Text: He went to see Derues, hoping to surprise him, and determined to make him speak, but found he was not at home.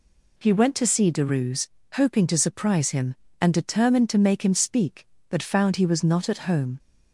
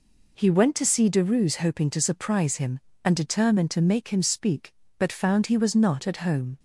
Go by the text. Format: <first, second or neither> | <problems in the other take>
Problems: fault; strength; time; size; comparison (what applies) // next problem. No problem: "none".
neither | none